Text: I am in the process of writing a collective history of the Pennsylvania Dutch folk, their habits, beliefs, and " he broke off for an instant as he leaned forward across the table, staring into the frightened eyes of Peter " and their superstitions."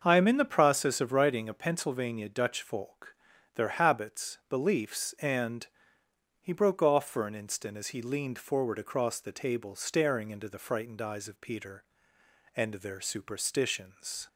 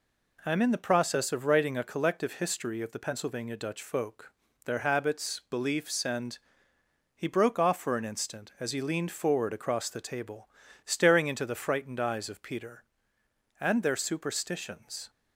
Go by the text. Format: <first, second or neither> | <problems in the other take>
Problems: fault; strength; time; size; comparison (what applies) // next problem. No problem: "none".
second | starts louder than the rest; until 1.0 s; 6.5 dB // skips "collective history of the"; at 1.5 s